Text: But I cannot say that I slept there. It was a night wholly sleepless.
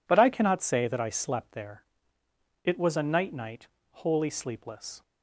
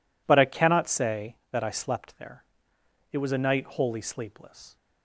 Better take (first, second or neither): second